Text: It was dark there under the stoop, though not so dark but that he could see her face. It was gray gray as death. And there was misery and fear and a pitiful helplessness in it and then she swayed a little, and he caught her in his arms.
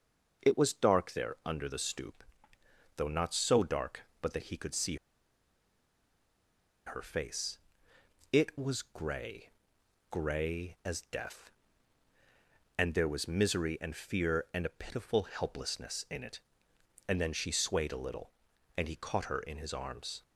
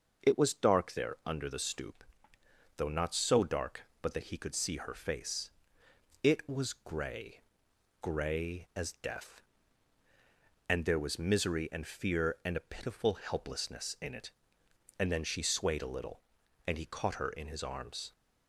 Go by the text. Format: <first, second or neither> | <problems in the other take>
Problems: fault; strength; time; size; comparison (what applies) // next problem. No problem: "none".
second | starts louder than the rest; noticeable; until 1.5 s; 6 dB; noticeable in the second // pauses between "see" and "her"; strong; at 4.9 s; 1.9 s long // pauses between "gray" and "gray"; noticeable; at 9.5 s; 0.62 s long; noticeable in the second